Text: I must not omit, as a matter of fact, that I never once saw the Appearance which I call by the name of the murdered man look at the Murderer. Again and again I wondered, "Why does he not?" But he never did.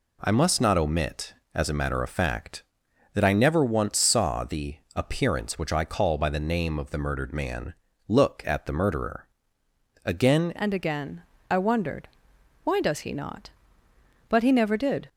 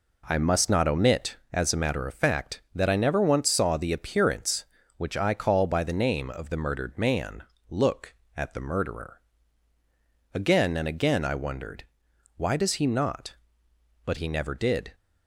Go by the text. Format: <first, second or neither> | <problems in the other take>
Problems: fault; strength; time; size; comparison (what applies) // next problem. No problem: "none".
second | pauses between "the" and "Appearance"; slight; at 4.7 s; 0.20 s long // pauses between "man" and "look"; slight; at 7.7 s; 0.34 s long; slight in the second // changes voice at "and"; from 10.5 s on; 4.5 s long // pauses between "again" and "I"; slight; at 11.2 s; 0.28 s long